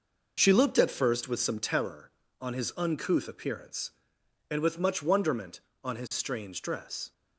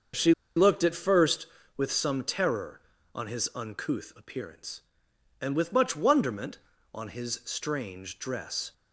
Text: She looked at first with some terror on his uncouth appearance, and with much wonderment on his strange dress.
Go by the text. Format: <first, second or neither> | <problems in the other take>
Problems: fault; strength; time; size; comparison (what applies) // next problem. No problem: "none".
first | starts louder than the rest; until 1.3 s; 6.5 dB // pauses between "She" and "looked"; slight; at 0.3 s; 0.23 s long